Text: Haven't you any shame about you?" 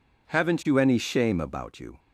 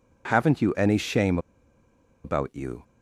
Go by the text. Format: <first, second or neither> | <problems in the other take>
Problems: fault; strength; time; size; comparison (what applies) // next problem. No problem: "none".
first | pauses between "shame" and "about"; noticeable; at 1.3 s; 0.86 s long